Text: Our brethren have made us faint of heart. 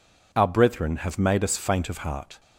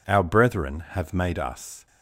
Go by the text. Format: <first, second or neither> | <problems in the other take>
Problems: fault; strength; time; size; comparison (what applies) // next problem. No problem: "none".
first | stops before "faint of heart"; at 1.8 s